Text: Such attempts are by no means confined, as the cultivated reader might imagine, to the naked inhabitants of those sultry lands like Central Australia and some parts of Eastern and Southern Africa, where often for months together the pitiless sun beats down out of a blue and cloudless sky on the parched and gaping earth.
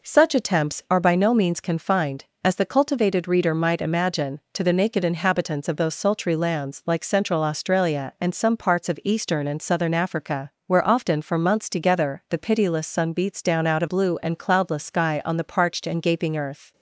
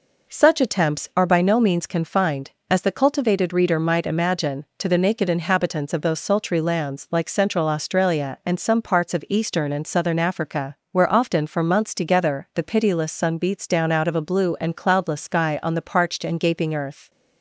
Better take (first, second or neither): second